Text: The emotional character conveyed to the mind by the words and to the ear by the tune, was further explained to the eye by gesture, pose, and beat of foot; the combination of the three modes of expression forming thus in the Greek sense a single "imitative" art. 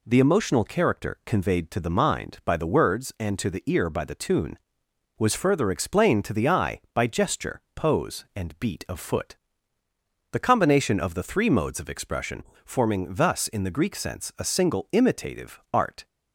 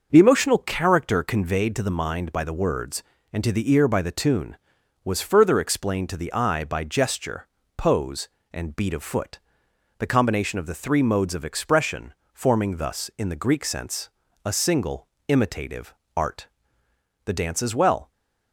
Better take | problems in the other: first | starts louder than the rest; until 1.1 s; 6.5 dB // pauses between "expression" and "forming"; slight; at 12.1 s; 0.20 s long; slight in the first // pauses between "sense" and "a"; slight; at 14.0 s; 0.34 s long // pauses between "single" and "imitative"; slight; at 15.0 s; 0.22 s long // pauses between "imitative" and "art"; slight; at 15.9 s; 0.24 s long // goes on to say "The dance as well"; noticeable; from 17.2 s on; 0.88 s long

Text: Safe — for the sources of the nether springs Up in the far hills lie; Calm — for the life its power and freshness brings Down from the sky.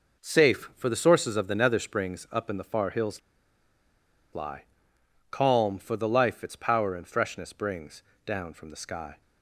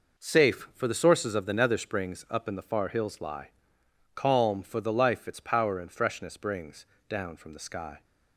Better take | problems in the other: second | pauses between "hills" and "lie"; at 3.2 s; 1.1 s long // pauses between "brings" and "Down"; slight; at 8.0 s; 0.22 s long; slight in the second

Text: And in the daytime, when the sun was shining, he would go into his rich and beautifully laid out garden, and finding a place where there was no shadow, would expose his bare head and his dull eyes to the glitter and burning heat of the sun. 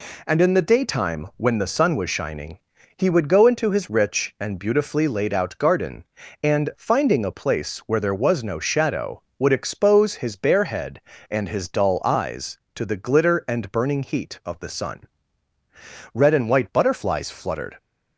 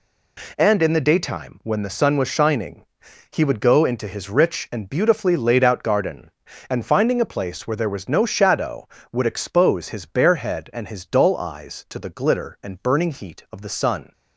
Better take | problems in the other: second | goes on to say "Red and white butterflies fluttered"; from 16.1 s on; 1.6 s long

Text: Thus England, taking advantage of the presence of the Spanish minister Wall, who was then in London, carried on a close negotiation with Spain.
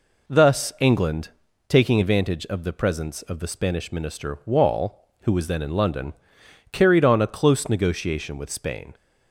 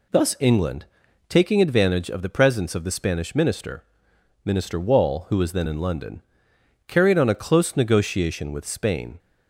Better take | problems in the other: first | says "minister" twice; at 4.4 s

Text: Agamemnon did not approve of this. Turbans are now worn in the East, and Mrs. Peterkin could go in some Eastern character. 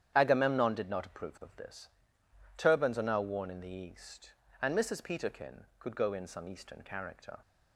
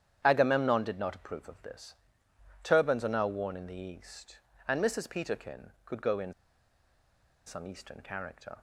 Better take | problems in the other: first | starts louder than the rest; strong; until 1.2 s; 9.5 dB; strong in the first // pauses between "in" and "some"; at 6.3 s; 1.1 s long

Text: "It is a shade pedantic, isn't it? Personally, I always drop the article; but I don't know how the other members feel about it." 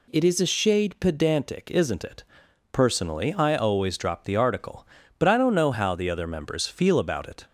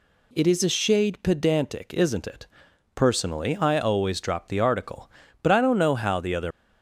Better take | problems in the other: first | stops before "members feel about it"; at 6.5 s

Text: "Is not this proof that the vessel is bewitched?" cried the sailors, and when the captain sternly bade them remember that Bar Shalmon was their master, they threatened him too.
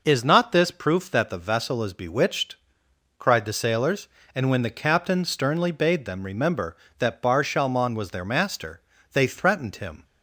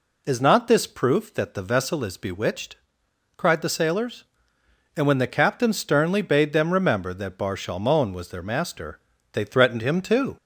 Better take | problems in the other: second | stops before "too"; at 10.0 s

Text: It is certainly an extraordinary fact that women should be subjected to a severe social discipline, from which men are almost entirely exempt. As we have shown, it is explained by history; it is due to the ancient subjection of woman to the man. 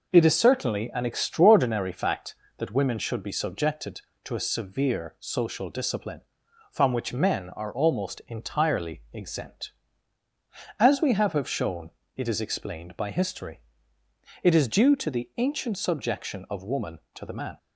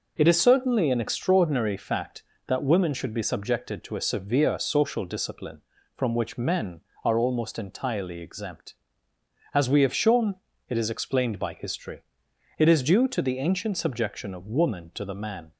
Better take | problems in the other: second | says "have" twice; at 11.3 s

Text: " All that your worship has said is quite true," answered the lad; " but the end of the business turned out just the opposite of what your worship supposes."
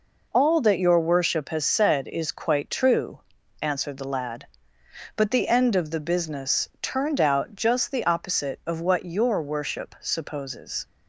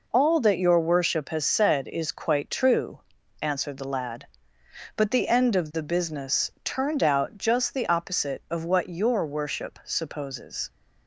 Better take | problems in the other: neither | none

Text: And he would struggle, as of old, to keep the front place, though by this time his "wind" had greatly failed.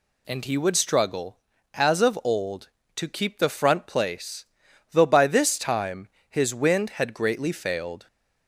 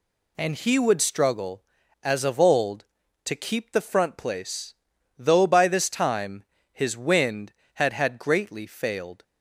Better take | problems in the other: first | pauses between "time" and "his"; slight; at 6.4 s; 0.30 s long; slight in the first // says "had" twice; at 7.9 s

